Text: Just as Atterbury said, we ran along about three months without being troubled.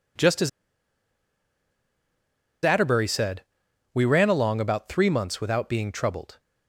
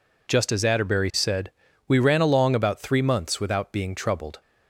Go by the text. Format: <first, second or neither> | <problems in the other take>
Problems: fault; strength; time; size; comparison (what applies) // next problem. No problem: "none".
second | pauses between "as" and "Atterbury"; strong; at 0.4 s; 2.1 s long